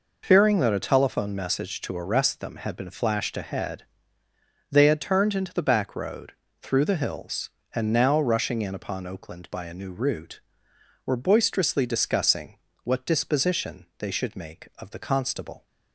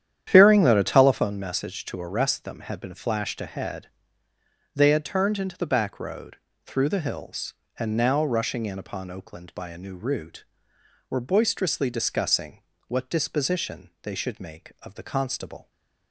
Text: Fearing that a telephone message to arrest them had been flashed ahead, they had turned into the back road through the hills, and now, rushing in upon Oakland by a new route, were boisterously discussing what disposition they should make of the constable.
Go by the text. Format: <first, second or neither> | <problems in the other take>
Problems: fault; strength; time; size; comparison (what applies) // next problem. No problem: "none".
first | starts louder than the rest; strong; until 1.3 s; 10 dB // pauses between "road" and "through"; slight; at 6.3 s; 0.30 s long; slight in the first // pauses between "discussing" and "what"; slight; at 12.6 s; 0.28 s long; slight in the first